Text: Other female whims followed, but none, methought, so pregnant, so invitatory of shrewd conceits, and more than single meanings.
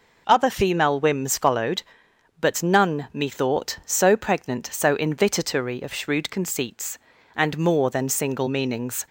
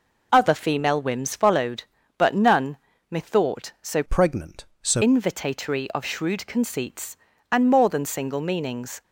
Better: first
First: none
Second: changes voice from "pregnant" to "so"; from 4.0 to 5.0 s; 1.0 s long

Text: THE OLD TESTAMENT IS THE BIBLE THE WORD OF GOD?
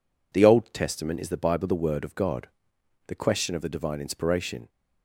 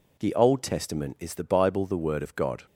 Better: second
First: goes on to say "The question of the divine inspiration"; from 3.0 s on; 1.6 s long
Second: none

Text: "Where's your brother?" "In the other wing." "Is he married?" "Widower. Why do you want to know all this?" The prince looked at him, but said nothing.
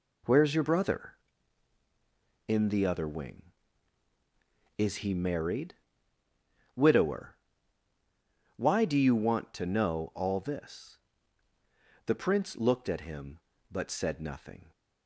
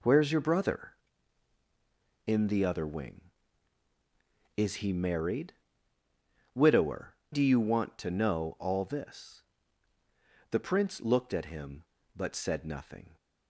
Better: first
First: none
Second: skips "Why"; at 7.2 s

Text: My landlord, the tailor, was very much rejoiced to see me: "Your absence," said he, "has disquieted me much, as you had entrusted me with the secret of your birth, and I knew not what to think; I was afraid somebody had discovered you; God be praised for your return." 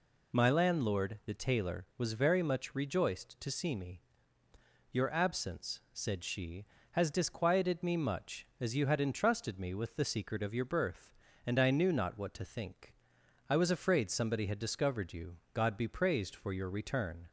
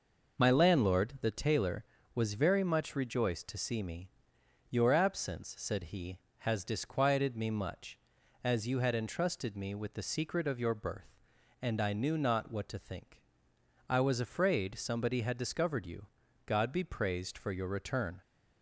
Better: second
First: says "she" for "he"; at 6.2 s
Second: none

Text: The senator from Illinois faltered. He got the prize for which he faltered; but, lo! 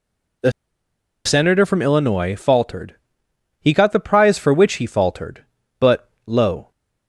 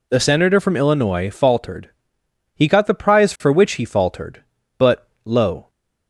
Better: second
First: pauses between "The" and "senator"; noticeable; at 0.5 s; 0.75 s long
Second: none

